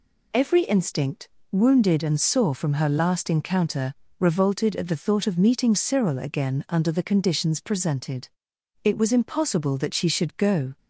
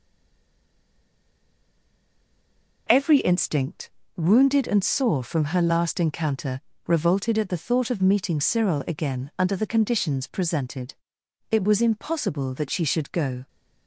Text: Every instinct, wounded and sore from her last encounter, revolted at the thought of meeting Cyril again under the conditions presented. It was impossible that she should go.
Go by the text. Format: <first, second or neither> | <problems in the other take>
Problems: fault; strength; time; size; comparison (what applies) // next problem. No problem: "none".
first | stays silent before the first word; strong; until 2.8 s; 2.8 s long